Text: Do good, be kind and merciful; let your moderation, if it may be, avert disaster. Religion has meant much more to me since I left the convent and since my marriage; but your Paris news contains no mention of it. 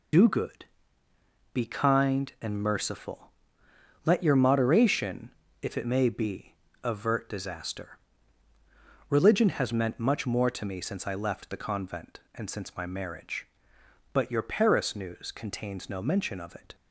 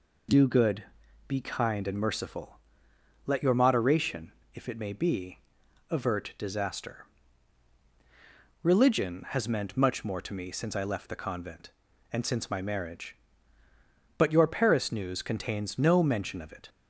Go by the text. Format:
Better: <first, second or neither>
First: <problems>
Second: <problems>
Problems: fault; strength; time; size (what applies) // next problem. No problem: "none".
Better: second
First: loses the start of "Do"; at 0.1 s; 60 ms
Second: none